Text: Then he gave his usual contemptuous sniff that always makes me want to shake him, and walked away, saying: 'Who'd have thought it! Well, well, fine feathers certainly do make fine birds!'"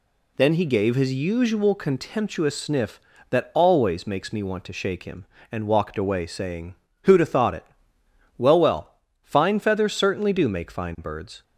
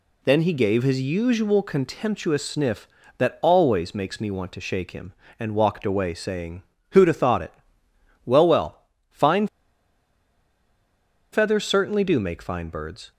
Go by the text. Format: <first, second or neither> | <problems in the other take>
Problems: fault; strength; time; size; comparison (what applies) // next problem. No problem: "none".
first | pauses between "fine" and "feathers"; strong; at 9.4 s; 1.8 s long